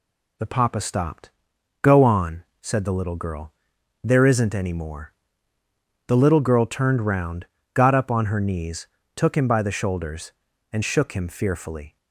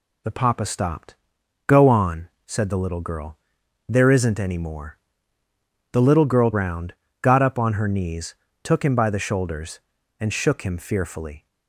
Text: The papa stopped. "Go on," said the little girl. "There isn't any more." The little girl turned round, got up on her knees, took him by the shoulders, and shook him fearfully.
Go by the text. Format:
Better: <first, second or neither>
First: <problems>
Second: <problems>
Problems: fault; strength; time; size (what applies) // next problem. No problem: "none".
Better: first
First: none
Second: skips "turned"; at 6.5 s